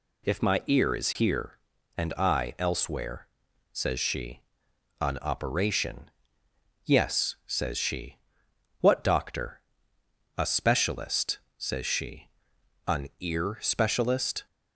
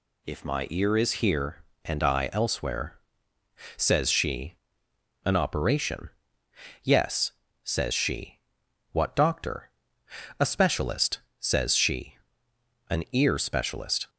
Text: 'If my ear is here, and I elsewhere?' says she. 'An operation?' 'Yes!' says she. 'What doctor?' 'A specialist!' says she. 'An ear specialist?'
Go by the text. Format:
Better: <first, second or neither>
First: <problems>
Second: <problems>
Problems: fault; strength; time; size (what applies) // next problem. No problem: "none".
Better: neither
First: none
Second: none